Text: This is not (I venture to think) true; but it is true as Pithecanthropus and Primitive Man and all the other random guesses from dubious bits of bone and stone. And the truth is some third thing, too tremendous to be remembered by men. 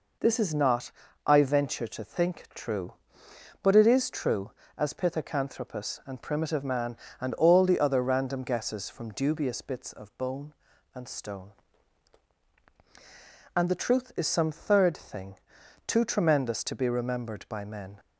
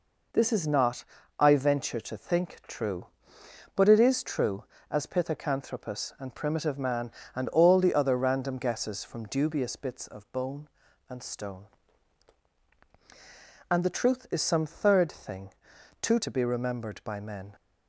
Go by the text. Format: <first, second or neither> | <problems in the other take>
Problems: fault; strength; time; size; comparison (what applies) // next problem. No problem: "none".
first | skips "tremendous"; at 16.1 s